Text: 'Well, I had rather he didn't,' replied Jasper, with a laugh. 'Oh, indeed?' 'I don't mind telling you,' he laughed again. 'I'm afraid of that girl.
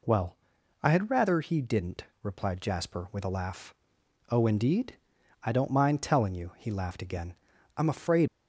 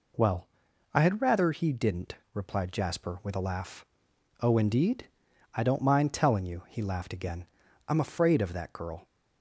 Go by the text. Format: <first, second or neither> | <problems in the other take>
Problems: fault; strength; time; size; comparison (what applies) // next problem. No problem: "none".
second | stops before "of that girl"; at 8.2 s